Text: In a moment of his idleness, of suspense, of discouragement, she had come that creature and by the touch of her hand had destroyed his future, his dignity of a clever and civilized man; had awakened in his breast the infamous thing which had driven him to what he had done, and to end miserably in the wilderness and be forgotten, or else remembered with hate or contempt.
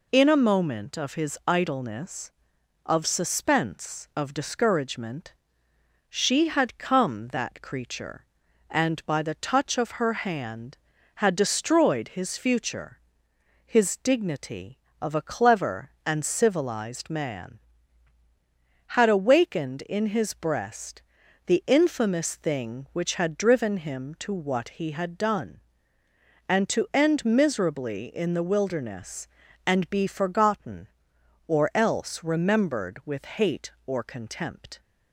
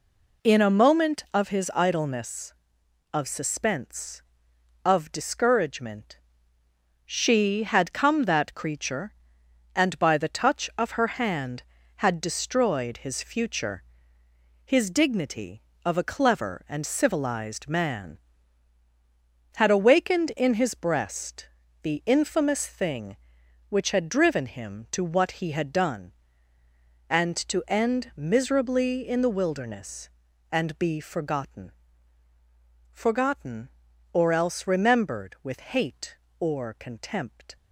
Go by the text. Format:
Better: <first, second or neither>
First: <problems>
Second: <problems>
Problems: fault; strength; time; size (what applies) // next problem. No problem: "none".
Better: first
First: pauses between "breast" and "the"; at 21.0 s; 0.42 s long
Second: pauses between "breast" and "the"; slight; at 21.4 s; 0.34 s long // says "forgotten" twice; at 32.9 s